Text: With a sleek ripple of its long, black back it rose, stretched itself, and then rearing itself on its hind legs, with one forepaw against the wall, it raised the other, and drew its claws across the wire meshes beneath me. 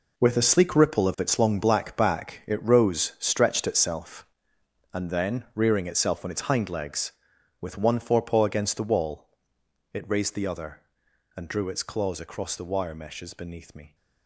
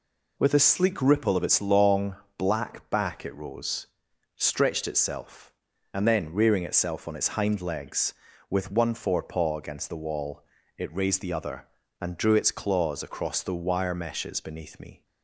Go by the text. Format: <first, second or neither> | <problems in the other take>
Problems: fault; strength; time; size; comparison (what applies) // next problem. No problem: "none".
second | gets quieter; strong; throughout; 11.5 dB